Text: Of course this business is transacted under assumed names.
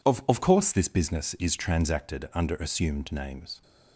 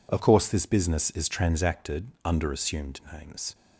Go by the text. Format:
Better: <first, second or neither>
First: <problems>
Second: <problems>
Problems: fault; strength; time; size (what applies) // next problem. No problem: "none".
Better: second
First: says "Of" twice; at 0.2 s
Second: none